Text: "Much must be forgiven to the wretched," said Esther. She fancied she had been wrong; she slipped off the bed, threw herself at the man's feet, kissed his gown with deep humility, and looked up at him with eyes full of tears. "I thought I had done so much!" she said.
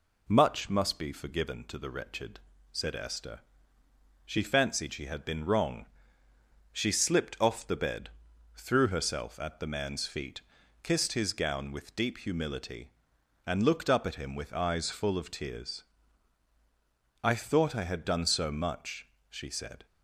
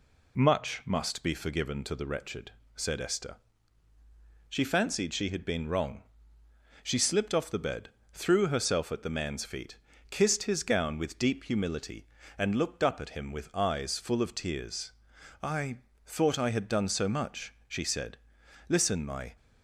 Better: first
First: none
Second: pauses between "I" and "thought"; slight; at 15.7 s; 0.26 s long // goes on to say "Listen my"; noticeable; from 18.6 s on; 0.68 s long

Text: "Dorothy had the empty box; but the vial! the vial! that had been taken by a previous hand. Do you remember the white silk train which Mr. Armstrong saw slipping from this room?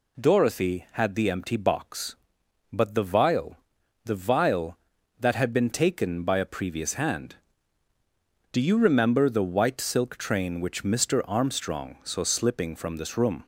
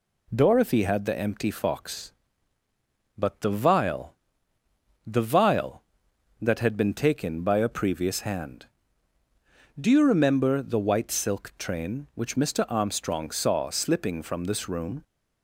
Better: first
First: none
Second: says "fox" for "box"; at 1.4 s

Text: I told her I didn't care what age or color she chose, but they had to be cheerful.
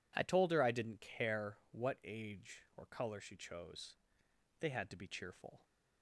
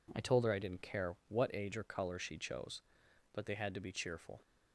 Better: second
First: skips "but"; at 4.2 s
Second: none

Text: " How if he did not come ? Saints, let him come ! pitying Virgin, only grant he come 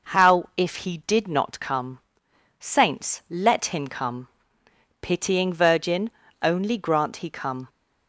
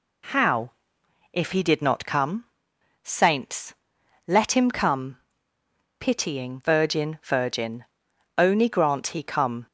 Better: first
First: none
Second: pauses between "How" and "if"; noticeable; at 0.7 s; 0.64 s long // says "Virgin" twice; at 7.2 s

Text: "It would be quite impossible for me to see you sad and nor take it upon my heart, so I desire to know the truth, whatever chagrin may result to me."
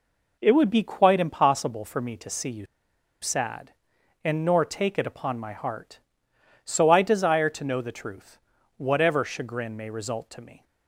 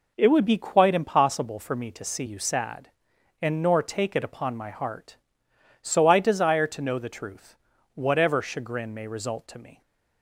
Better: second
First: pauses between "you" and "sad"; noticeable; at 2.6 s; 0.55 s long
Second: none

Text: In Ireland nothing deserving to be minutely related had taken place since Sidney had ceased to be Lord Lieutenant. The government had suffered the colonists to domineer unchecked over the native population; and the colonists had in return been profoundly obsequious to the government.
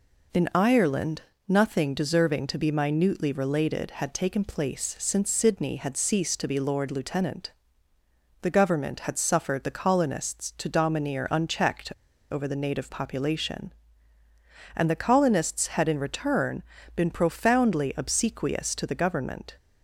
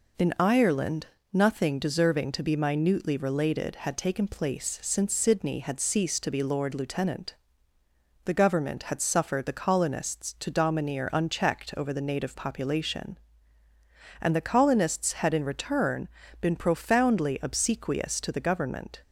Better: second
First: pauses between "Ireland" and "nothing"; slight; at 1.2 s; 0.26 s long // pauses between "unchecked" and "over"; at 11.9 s; 0.40 s long // pauses between "return" and "been"; slight; at 16.6 s; 0.32 s long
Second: pauses between "Ireland" and "nothing"; slight; at 1.0 s; 0.26 s long // pauses between "return" and "been"; slight; at 16.0 s; 0.32 s long

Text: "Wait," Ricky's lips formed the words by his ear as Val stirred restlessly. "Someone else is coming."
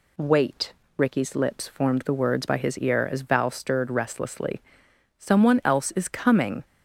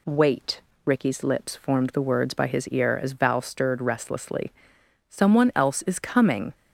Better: neither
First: none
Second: none

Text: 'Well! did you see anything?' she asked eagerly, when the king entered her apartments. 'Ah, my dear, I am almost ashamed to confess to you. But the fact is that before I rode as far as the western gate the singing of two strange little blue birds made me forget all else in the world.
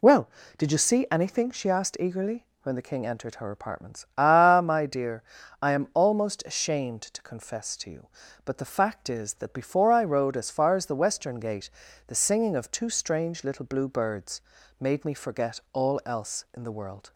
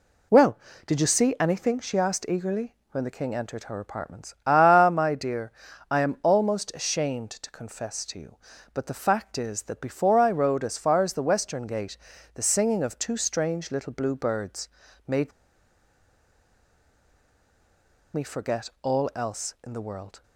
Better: first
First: pauses between "gate" and "the"; at 11.6 s; 0.38 s long // pauses between "birds" and "made"; at 14.4 s; 0.40 s long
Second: pauses between "gate" and "the"; at 11.9 s; 0.38 s long // pauses between "birds" and "made"; at 14.6 s; 0.40 s long // pauses between "made" and "me"; strong; at 15.3 s; 2.8 s long

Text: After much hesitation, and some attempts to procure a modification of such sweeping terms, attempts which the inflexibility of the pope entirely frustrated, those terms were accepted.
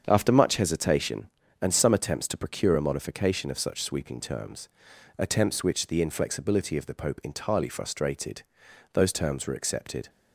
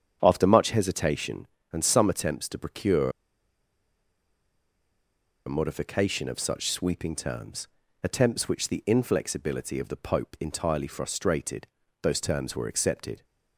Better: first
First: starts louder than the rest; strong; until 1.0 s; 7.5 dB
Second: starts louder than the rest; strong; until 1.2 s; 8 dB // pauses between "procure" and "a"; strong; at 3.0 s; 2.3 s long

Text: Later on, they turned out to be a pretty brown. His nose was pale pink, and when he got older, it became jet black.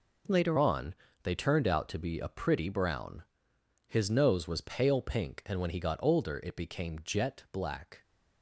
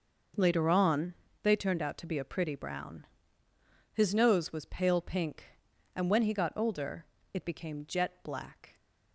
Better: second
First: changes voice at "on"; from 0.5 s on; 7.5 s long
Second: none

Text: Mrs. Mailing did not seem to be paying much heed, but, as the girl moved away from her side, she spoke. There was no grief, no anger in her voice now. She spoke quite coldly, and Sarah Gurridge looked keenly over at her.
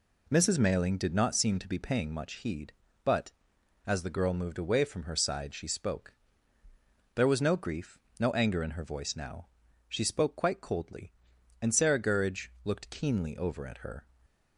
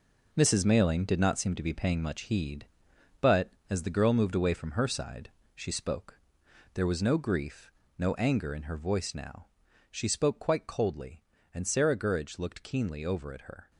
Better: first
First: none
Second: gets quieter; strong; throughout; 9 dB

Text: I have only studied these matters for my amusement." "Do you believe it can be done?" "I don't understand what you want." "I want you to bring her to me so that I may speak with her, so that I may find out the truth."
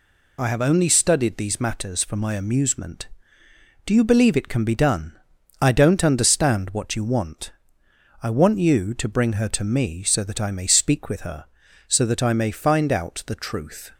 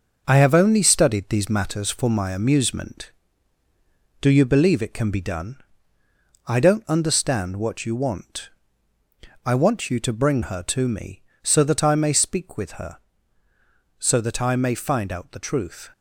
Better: first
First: none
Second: gets quieter; noticeable; throughout; 5.5 dB

